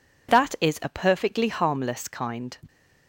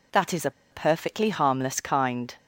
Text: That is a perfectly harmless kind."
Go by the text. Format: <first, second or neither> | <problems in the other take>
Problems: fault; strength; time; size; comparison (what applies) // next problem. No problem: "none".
first | pauses between "a" and "perfectly"; slight; at 0.4 s; 0.21 s long